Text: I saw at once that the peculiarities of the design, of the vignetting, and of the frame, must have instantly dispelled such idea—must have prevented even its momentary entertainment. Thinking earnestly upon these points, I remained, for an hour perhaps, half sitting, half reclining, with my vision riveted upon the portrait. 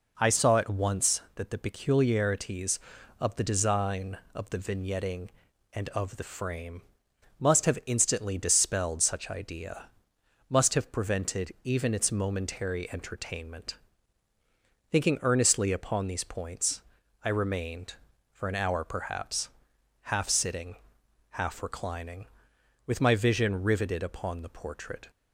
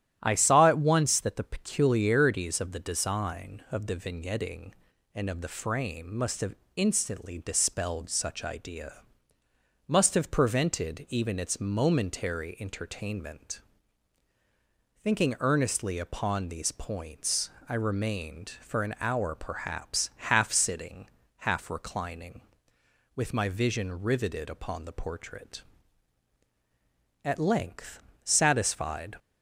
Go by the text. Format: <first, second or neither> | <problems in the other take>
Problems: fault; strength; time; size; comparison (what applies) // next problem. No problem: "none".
first | starts louder than the rest; strong; until 1.2 s; 12 dB // pauses between "have" and "instantly"; slight; at 6.5 s; 0.20 s long // goes on to say "At length satisfied"; strong; from 27.2 s on; 1.9 s long